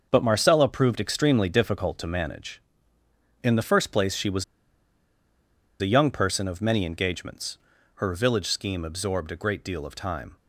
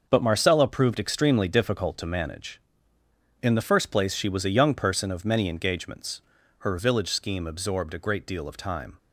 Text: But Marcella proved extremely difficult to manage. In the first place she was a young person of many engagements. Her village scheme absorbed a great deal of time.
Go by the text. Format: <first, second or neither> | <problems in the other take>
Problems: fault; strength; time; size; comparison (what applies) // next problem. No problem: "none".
second | starts louder than the rest; until 1.1 s; 6 dB; also in the second // pauses between "was" and "a"; strong; at 4.4 s; 1.3 s long